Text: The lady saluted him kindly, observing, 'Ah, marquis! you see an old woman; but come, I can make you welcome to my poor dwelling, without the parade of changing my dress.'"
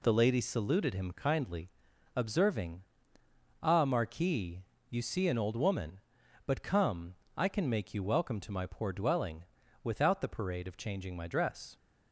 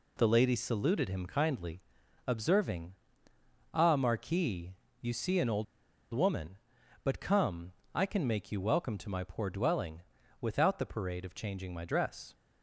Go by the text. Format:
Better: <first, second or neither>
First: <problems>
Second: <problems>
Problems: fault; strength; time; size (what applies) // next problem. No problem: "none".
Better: first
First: none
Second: pauses between "old" and "woman"; noticeable; at 5.6 s; 0.48 s long